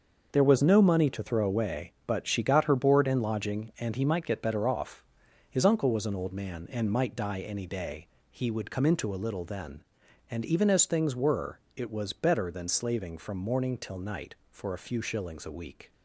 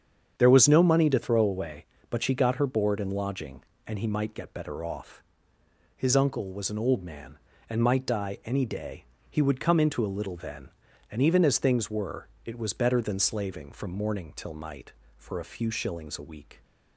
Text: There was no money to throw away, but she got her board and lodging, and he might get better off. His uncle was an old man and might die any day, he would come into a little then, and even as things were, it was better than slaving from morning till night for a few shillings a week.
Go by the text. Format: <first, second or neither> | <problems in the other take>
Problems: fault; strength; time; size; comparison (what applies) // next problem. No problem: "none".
neither | starts louder than the rest; the same in both